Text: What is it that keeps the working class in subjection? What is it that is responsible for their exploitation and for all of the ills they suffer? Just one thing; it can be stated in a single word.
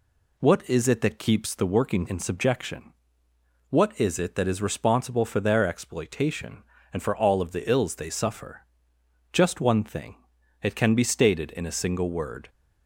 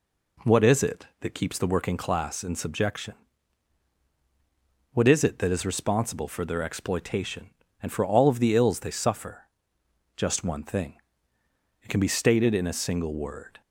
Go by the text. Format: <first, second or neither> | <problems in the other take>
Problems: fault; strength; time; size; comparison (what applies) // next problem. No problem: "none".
second | skips "class"; at 2.0 s